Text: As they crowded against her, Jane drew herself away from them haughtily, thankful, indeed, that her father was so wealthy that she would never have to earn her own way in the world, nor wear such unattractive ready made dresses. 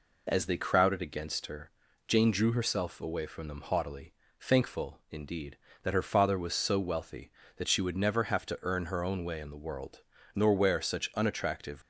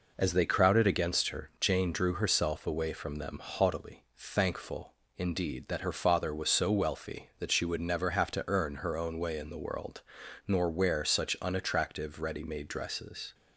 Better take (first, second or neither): second